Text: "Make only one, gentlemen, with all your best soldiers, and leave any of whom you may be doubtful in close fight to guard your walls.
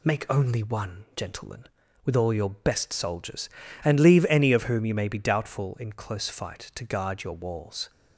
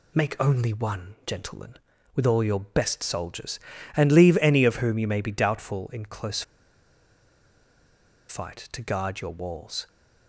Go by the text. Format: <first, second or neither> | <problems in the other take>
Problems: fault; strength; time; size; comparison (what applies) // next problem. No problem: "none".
first | pauses between "close" and "fight"; strong; at 6.4 s; 1.8 s long